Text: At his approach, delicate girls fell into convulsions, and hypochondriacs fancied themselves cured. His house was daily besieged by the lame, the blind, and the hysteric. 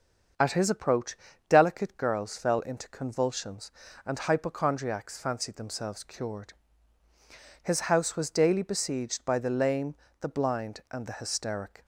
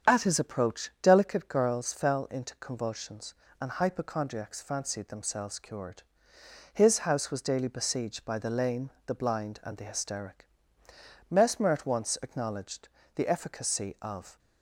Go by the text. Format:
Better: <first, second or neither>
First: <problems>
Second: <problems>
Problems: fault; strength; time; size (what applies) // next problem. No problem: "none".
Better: first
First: starts louder than the rest; until 1.6 s; 7 dB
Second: starts louder than the rest; strong; until 1.1 s; 8 dB // goes on to say "Mesmer at once acknowledged the efficacy of"; strong; from 11.3 s on; 3.0 s long